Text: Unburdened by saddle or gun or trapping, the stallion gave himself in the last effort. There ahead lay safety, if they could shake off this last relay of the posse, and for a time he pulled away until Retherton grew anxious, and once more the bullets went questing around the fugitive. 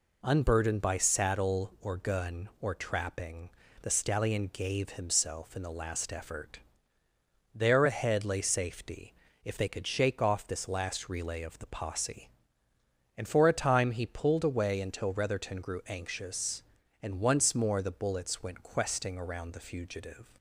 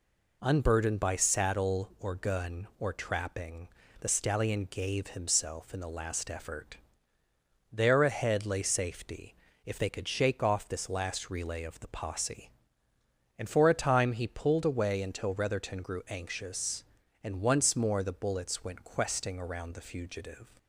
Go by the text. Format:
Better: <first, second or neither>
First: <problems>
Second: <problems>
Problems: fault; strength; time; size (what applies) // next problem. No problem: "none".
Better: neither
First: none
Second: none